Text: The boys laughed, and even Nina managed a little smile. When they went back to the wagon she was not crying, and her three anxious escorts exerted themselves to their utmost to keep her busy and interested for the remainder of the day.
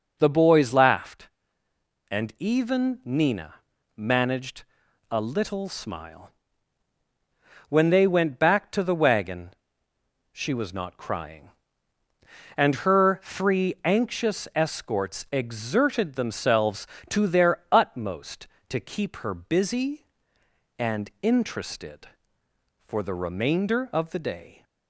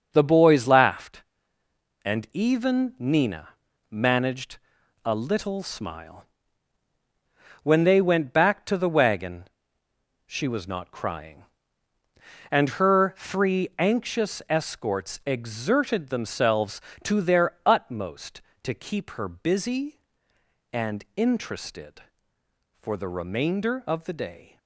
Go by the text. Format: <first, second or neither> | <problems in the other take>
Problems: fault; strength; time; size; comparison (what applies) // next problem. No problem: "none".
first | gets quieter; strong; throughout; 8 dB // pauses between "Nina" and "managed"; at 3.4 s; 0.40 s long; also in the first // pauses between "managed" and "a"; noticeable; at 4.5 s; 0.46 s long; noticeable in the first // pauses between "wagon" and "she"; noticeable; at 9.4 s; 0.82 s long; noticeable in the first